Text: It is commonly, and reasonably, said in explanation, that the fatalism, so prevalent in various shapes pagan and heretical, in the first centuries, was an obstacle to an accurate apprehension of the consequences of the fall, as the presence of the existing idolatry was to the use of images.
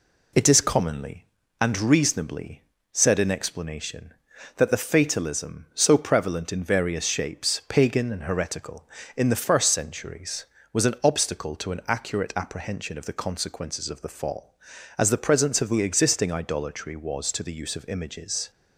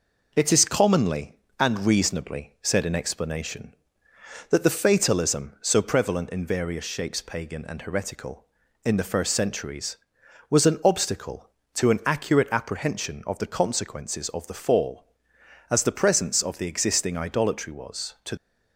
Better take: first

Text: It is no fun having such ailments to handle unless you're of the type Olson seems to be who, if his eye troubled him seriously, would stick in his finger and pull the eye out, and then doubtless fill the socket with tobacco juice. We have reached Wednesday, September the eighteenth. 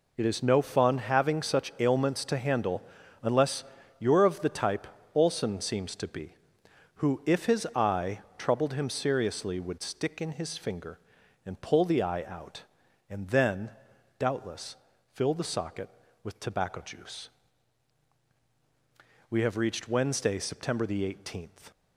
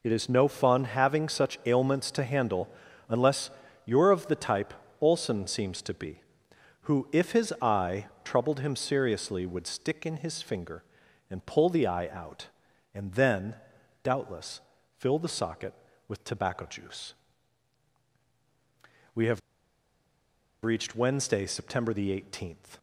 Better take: first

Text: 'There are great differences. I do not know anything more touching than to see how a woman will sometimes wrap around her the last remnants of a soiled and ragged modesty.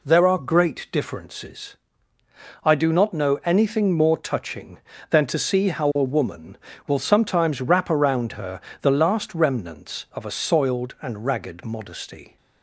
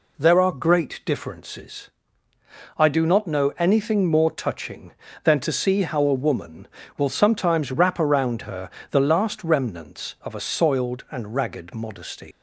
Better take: first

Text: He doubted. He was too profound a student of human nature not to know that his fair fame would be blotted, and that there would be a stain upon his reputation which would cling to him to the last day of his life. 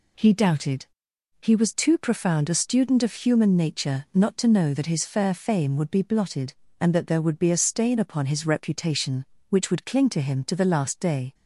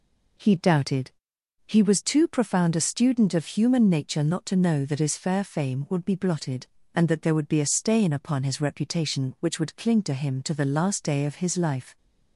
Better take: second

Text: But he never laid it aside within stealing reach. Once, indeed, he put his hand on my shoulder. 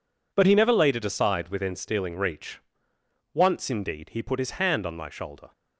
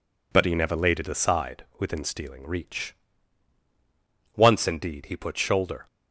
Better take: first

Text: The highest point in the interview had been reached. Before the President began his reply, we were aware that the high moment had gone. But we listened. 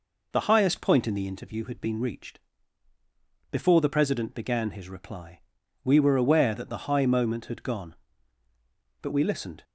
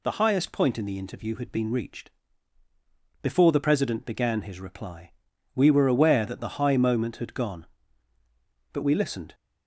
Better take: second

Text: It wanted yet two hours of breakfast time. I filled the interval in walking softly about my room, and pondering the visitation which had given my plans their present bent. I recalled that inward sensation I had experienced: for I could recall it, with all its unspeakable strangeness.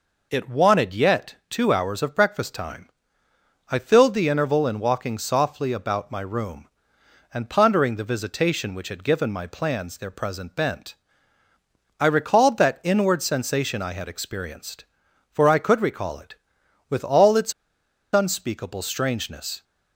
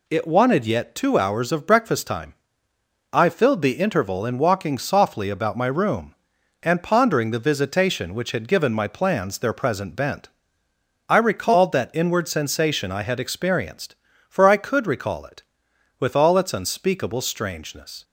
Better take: second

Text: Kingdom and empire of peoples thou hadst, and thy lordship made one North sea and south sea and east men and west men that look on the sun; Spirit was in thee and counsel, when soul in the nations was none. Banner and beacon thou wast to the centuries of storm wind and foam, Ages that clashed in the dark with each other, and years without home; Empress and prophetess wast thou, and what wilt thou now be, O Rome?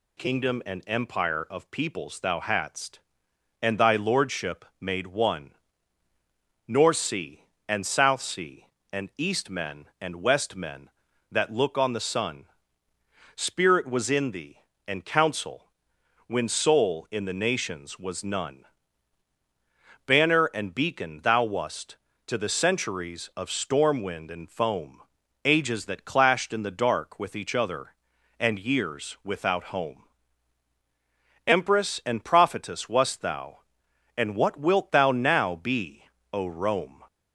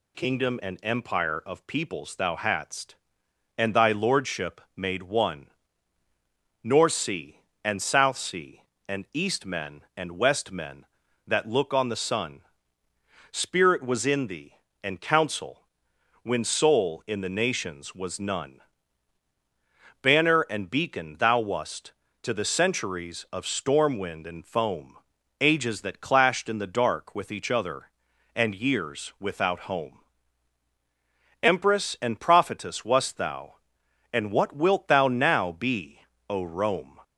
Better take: neither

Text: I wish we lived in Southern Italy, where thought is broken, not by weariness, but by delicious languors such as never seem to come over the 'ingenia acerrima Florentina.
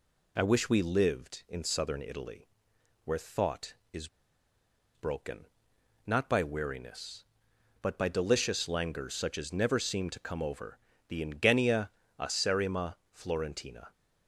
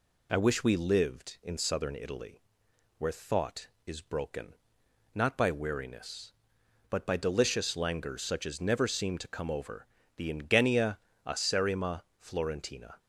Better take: second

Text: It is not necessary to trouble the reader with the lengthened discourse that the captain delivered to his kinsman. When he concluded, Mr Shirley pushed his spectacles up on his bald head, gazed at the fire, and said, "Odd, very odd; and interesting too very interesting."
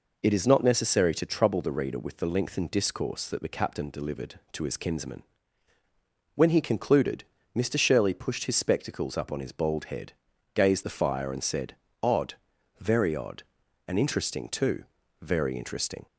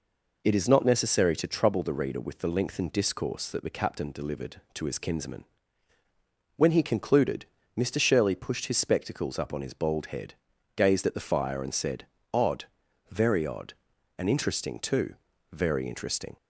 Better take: second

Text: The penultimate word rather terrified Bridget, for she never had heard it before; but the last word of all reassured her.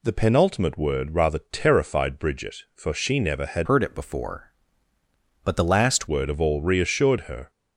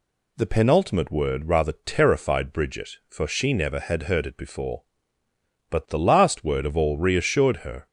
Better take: second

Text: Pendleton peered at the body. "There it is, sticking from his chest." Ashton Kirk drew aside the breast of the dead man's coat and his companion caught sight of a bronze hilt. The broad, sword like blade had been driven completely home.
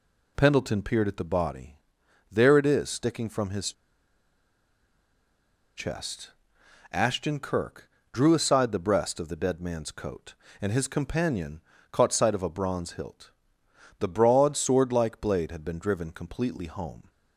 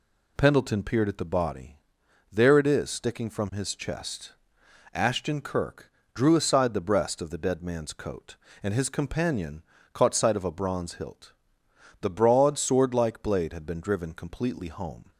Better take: second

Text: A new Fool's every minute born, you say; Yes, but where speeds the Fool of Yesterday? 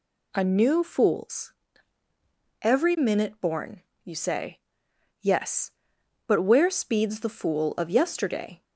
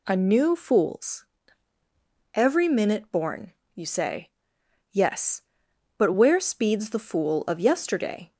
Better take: neither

